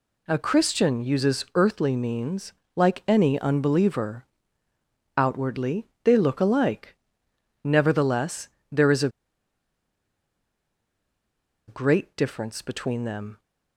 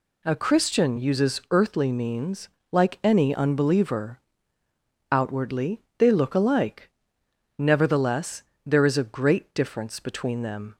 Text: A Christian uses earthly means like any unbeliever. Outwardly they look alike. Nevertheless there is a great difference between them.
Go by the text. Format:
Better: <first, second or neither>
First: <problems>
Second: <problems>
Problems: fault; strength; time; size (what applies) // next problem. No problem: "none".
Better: second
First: pauses between "means" and "like"; slight; at 2.5 s; 0.24 s long // pauses between "Outwardly" and "they"; slight; at 5.8 s; 0.18 s long // pauses between "Nevertheless" and "there"; slight; at 8.4 s; 0.24 s long // pauses between "a" and "great"; strong; at 9.0 s; 2.5 s long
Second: pauses between "means" and "like"; slight; at 2.4 s; 0.24 s long // pauses between "Outwardly" and "they"; slight; at 5.8 s; 0.18 s long // pauses between "Nevertheless" and "there"; slight; at 8.4 s; 0.24 s long